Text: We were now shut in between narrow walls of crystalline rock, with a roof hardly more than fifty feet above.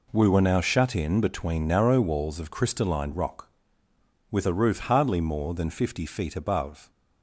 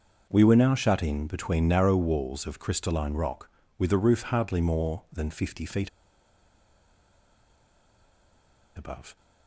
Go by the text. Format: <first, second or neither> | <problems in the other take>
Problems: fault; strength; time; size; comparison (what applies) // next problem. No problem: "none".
first | starts louder than the rest; until 1.3 s; 6.5 dB // pauses between "feet" and "above"; strong; at 5.8 s; 2.8 s long